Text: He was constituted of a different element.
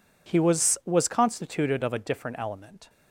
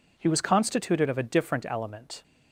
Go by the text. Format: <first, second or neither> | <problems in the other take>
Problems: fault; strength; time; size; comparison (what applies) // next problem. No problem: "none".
second | says "was" twice; at 0.8 s